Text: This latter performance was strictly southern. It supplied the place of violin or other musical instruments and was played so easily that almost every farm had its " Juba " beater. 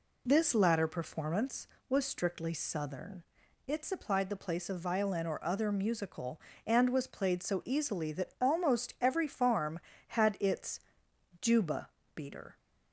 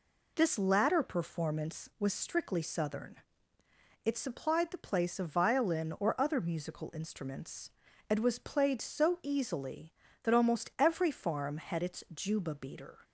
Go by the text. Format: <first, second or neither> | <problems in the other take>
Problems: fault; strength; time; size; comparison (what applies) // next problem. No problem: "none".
second | skips "instruments"; at 6.5 s